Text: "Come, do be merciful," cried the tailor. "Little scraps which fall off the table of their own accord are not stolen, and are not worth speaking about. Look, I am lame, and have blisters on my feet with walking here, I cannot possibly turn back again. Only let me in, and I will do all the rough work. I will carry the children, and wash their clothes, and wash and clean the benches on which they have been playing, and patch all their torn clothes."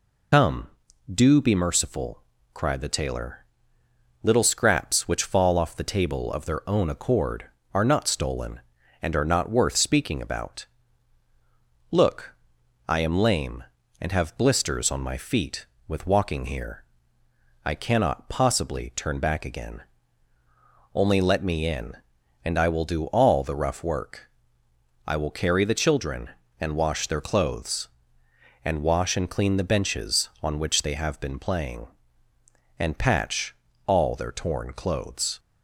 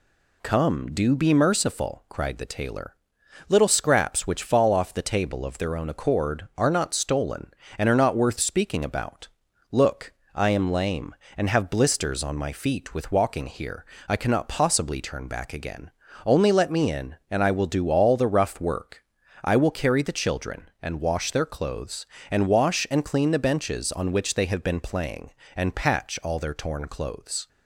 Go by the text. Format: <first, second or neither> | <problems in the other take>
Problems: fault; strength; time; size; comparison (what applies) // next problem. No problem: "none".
second | loses the start of "Come"; at 0.3 s; 75 ms // pauses between "patch" and "all"; slight; at 33.5 s; 0.32 s long